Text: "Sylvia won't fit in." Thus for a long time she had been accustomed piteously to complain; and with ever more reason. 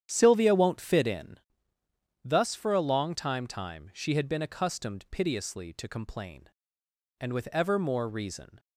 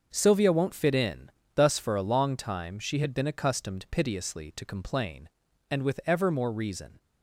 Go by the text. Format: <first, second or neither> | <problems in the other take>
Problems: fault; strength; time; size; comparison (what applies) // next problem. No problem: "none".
second | starts louder than the rest; strong; until 1.0 s; 9.5 dB; also in the second // says "time" twice; at 3.4 s